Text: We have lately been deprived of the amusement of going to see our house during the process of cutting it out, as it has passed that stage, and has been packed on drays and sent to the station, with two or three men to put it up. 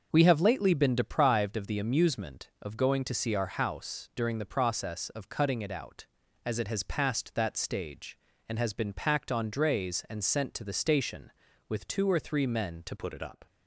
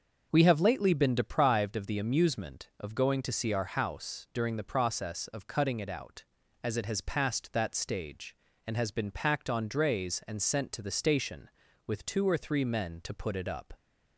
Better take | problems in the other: second | starts louder than the rest; until 1.1 s; 6.5 dB; also in the second // changes voice at "put"; from 12.9 s on; 0.5 s long

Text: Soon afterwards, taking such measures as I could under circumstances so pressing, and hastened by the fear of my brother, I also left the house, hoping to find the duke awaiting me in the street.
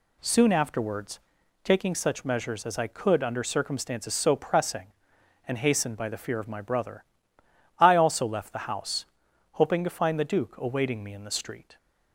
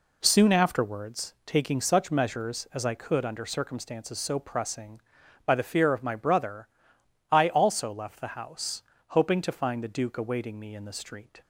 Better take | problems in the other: first | skips "and hastened"; at 5.2 s

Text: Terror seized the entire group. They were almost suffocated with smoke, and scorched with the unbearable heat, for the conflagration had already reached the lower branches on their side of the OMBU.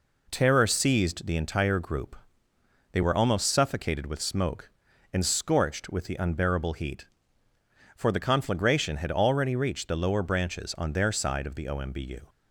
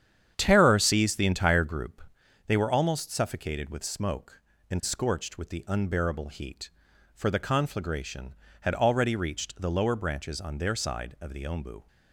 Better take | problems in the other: first | starts louder than the rest; strong; until 1.9 s; 9 dB

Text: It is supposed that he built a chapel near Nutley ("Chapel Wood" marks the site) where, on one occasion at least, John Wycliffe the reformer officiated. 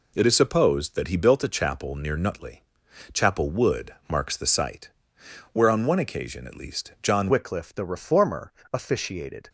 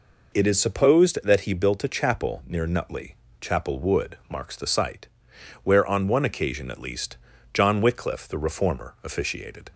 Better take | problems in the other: second | changes voice at "Wycliffe"; from 7.2 s on; 2.2 s long // pauses between "reformer" and "officiated"; slight; at 8.5 s; 0.22 s long

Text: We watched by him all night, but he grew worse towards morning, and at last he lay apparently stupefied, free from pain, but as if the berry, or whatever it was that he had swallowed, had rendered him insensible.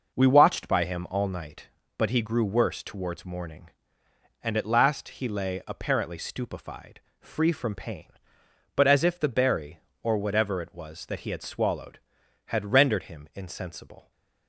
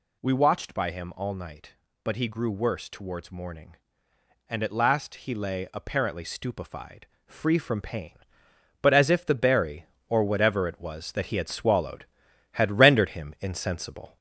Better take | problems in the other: first | gets louder; slight; throughout; 3 dB

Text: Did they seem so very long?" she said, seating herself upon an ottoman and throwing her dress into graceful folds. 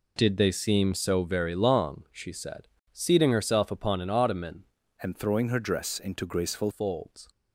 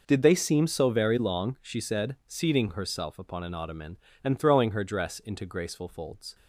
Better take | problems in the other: second | changes voice from "and" to "graceful"; from 5.0 to 6.6 s; 1.6 s long

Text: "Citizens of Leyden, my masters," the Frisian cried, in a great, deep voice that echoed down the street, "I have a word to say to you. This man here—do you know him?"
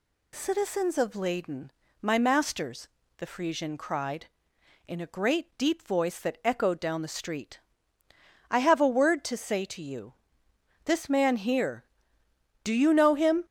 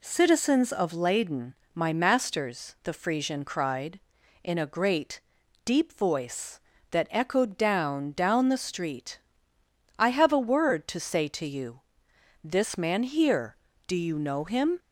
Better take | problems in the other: first | says "down" twice; at 8.1 s

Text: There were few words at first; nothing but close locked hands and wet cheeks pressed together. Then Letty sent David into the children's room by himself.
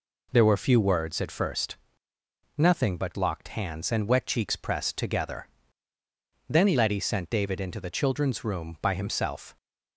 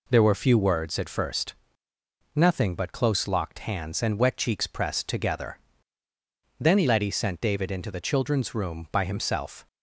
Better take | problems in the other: second | skips "close"; at 3.1 s

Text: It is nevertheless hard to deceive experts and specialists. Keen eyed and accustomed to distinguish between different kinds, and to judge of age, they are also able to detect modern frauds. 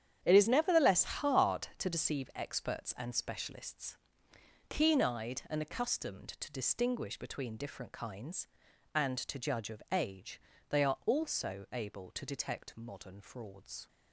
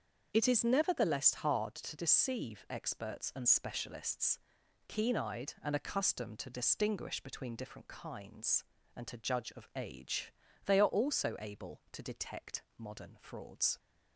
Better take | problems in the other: second | gets quieter; strong; throughout; 11.5 dB // starts louder than the rest; strong; until 1.2 s; 9 dB; also in the second

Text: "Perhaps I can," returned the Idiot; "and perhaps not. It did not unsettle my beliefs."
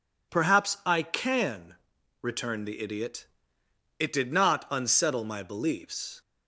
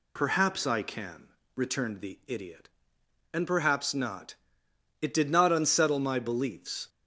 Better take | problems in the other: second | skips "and perhaps not"; at 3.6 s

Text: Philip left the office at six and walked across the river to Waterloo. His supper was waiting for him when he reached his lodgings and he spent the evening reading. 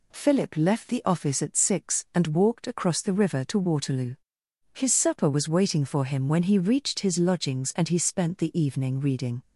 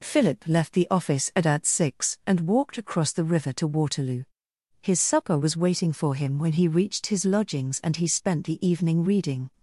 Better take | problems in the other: first | says "at" twice; at 1.4 s

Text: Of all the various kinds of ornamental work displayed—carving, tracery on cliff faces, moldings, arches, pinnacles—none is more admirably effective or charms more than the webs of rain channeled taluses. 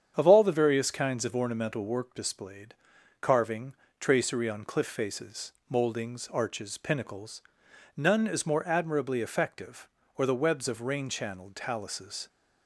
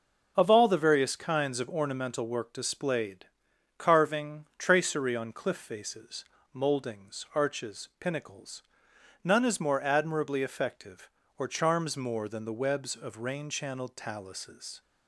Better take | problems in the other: second | starts louder than the rest; strong; until 1.1 s; 8 dB // skips "charms more than"; at 10.2 s

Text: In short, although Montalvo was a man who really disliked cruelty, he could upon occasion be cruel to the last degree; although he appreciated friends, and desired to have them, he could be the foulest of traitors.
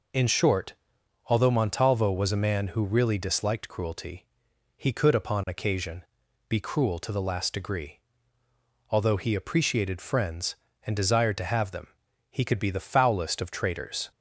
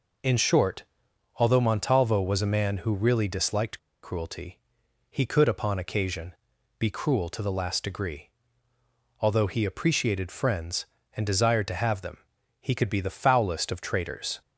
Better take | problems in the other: first | pauses between "disliked" and "cruelty"; slight; at 3.7 s; 0.25 s long // pauses between "occasion" and "be"; at 6.3 s; 0.44 s long; also in the first

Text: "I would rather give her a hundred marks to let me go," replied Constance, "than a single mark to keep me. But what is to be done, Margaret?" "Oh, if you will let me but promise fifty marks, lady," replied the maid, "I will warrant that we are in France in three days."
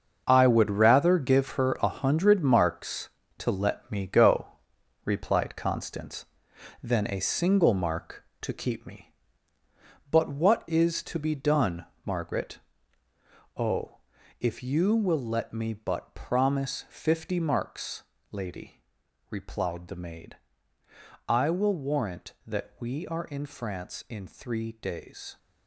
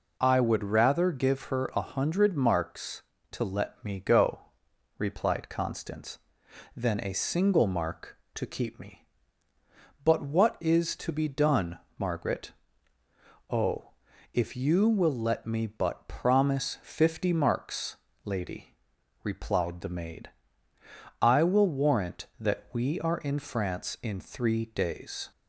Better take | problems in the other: second | gets quieter; strong; throughout; 10.5 dB

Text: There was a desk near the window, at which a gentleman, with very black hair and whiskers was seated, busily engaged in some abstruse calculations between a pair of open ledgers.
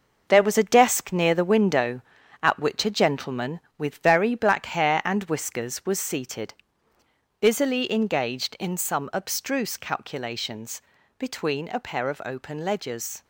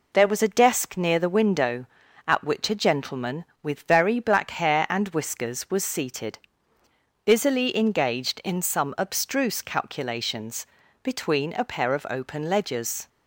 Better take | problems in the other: second | gets quieter; strong; throughout; 8 dB // pauses between "calculations" and "between"; slight; at 10.8 s; 0.36 s long; slight in the second

